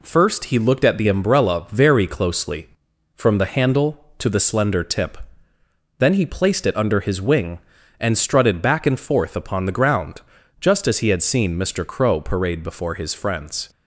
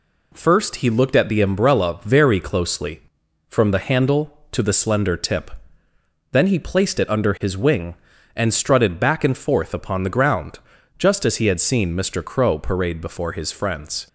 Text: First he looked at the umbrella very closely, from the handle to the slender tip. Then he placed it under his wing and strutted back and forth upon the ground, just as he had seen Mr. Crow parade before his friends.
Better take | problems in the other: neither | none

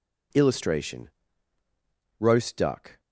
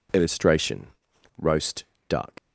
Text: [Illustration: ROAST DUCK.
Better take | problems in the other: first | pauses between "ROAST" and "DUCK"; slight; at 1.8 s; 0.24 s long // leaves "DUCK" unfinished; at 2.3 s; 100 ms

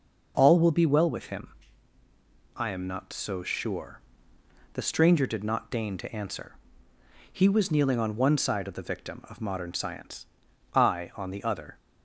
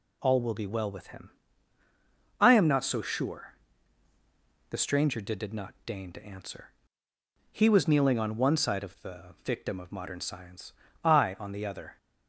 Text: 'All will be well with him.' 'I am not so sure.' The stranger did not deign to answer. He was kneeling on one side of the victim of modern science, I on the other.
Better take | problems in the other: first | says "did" twice; at 5.3 s

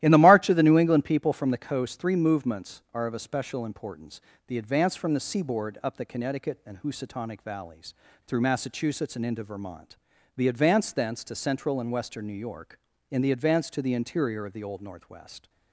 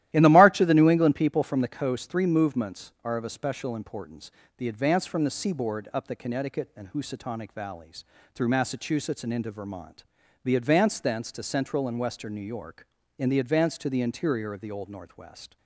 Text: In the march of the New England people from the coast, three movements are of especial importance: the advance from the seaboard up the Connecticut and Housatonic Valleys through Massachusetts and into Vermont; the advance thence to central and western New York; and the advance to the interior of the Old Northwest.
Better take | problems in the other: neither | starts louder than the rest; strong; the same in both // pauses between "Valleys" and "through"; slight; the same in both

